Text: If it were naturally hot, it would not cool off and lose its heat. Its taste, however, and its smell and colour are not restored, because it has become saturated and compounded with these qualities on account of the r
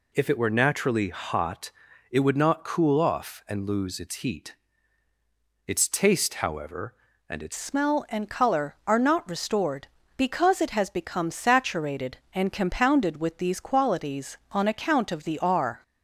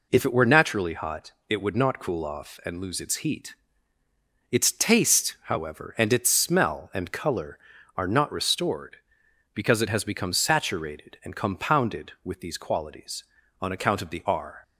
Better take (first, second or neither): second